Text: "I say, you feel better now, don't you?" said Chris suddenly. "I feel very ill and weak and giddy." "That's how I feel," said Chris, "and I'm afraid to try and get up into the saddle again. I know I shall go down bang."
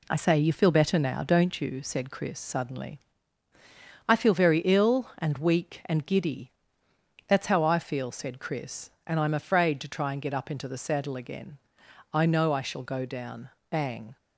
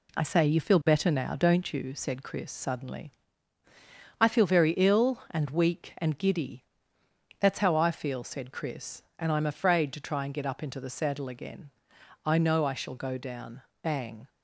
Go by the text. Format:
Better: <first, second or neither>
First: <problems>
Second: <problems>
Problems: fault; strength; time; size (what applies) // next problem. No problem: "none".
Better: neither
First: pauses between "down" and "bang"; slight; at 13.5 s; 0.20 s long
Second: pauses between "down" and "bang"; slight; at 13.6 s; 0.20 s long